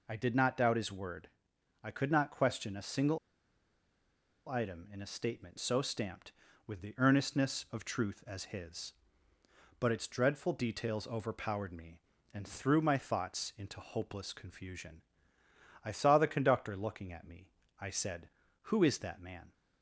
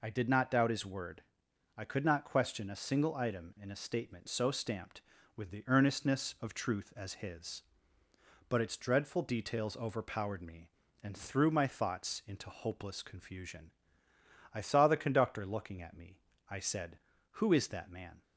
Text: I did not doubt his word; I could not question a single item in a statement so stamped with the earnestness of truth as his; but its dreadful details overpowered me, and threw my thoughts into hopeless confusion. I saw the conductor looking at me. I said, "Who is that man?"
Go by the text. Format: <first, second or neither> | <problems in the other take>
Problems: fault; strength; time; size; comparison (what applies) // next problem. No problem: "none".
second | pauses between "single" and "item"; strong; at 3.1 s; 1.3 s long